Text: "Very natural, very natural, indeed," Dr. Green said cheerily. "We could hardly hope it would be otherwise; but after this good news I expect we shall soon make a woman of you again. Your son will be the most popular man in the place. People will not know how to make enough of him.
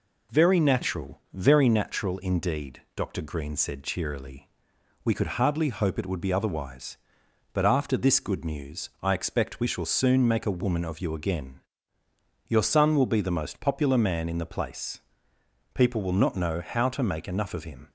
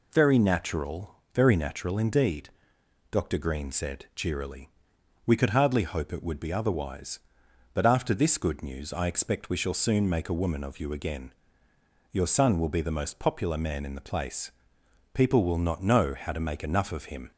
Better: neither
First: none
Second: none

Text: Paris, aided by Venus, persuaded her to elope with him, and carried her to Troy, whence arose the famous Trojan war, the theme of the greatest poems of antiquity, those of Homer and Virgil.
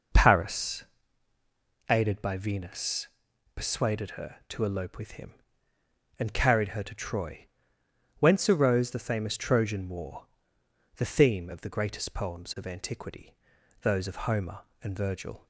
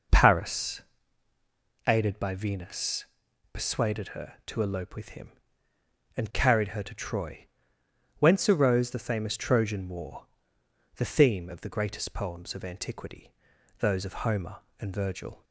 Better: neither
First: none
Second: none

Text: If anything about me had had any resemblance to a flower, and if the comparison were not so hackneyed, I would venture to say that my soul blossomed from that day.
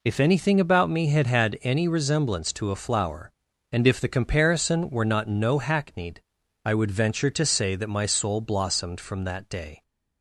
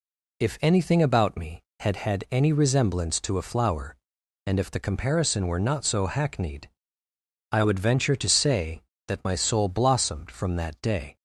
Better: second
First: says "no" for "so"; at 5.2 s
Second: none

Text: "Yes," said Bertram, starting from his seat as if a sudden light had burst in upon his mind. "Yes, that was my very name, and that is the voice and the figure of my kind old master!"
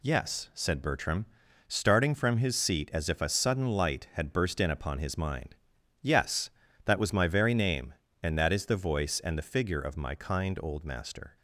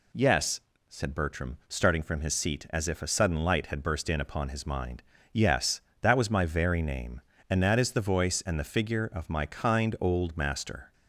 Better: neither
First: none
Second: none

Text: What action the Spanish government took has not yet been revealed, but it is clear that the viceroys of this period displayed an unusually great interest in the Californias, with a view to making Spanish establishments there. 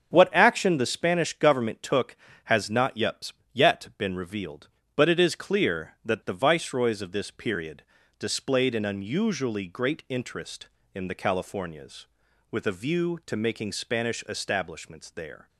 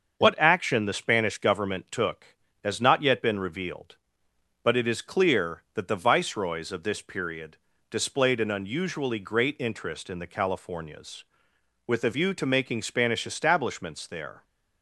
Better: second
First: starts louder than the rest; strong; until 1.1 s; 7.5 dB // says "yet" twice; at 3.5 s // pauses between "period" and "displayed"; slight; at 7.8 s; 0.36 s long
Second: starts louder than the rest; until 1.2 s; 6.5 dB // pauses between "period" and "displayed"; slight; at 7.5 s; 0.32 s long

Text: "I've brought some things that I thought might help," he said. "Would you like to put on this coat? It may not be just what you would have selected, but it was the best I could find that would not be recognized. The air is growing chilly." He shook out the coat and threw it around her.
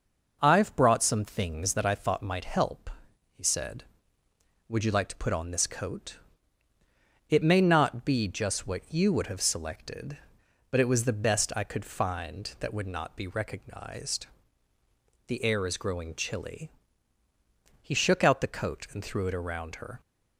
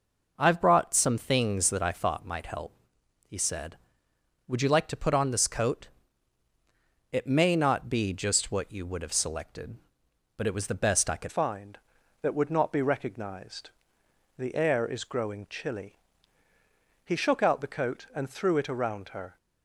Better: first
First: none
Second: changes voice at "find"; from 11.2 s on; 8.1 s long

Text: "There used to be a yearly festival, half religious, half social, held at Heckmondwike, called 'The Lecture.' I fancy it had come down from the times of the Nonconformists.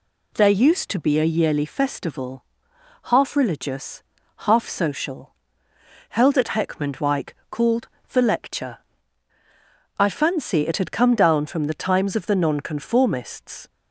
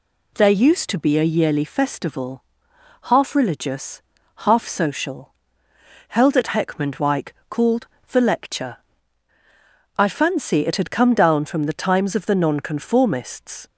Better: neither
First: pauses between "called" and "The"; slight; at 7.8 s; 0.22 s long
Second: pauses between "called" and "The"; slight; at 7.8 s; 0.22 s long

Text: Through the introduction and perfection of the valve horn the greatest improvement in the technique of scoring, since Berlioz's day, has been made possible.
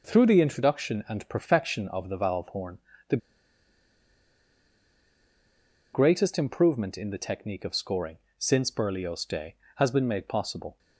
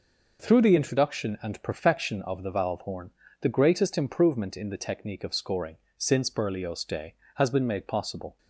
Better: second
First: pauses between "horn" and "the"; slight; at 2.7 s; 0.32 s long // pauses between "the" and "greatest"; strong; at 3.1 s; 2.7 s long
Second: pauses between "horn" and "the"; slight; at 3.0 s; 0.32 s long

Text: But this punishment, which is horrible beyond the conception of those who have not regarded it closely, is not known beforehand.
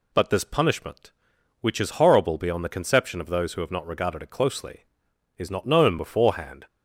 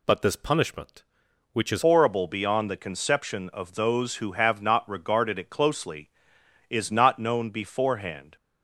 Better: first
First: none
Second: changes voice at "horrible"; from 1.8 s on; 6.5 s long

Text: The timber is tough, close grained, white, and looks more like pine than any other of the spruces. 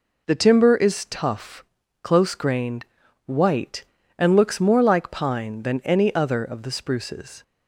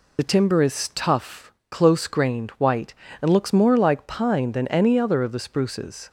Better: first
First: none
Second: loses the start of "The"; at 0.1 s; 40 ms

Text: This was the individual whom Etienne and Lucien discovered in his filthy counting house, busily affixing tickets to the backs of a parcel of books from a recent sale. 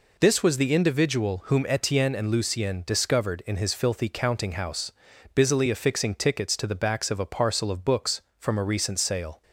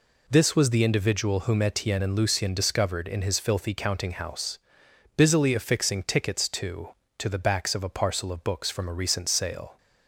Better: first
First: none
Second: says "to" twice; at 7.1 s

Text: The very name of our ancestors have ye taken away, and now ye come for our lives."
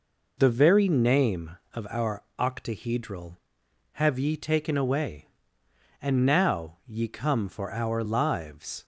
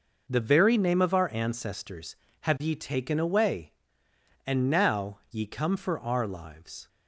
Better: second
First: says "octahedral" for "ancestors"; at 2.3 s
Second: none

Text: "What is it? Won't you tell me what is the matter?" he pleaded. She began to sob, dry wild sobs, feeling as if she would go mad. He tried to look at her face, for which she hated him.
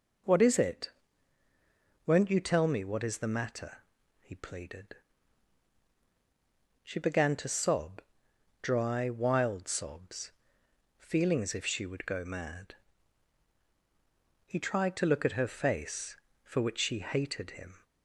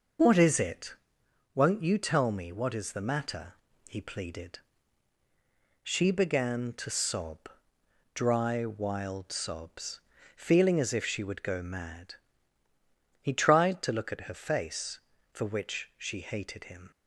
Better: neither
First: none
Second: none

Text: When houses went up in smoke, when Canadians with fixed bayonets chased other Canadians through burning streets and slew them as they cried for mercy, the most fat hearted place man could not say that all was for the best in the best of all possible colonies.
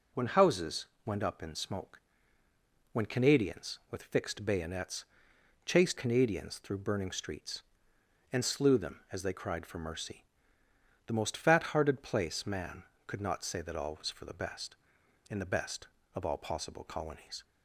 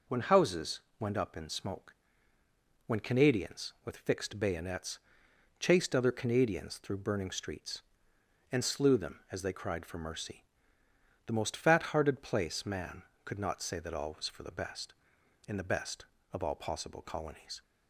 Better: second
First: pauses between "houses" and "went"; slight; at 0.8 s; 0.22 s long // pauses between "bayonets" and "chased"; noticeable; at 5.0 s; 0.60 s long // skips "other"; at 5.9 s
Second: pauses between "houses" and "went"; slight; at 0.7 s; 0.22 s long // pauses between "bayonets" and "chased"; noticeable; at 4.9 s; 0.60 s long

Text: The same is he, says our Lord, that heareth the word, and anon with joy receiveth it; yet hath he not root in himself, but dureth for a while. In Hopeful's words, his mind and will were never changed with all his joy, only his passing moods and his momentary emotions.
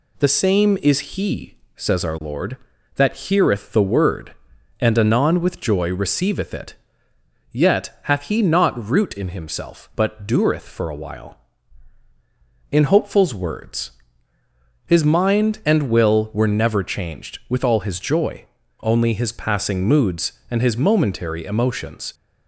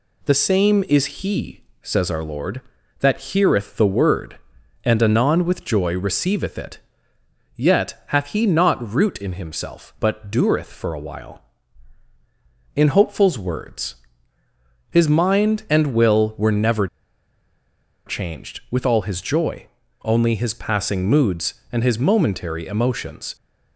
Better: first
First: none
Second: pauses between "never" and "changed"; at 16.8 s; 1.2 s long

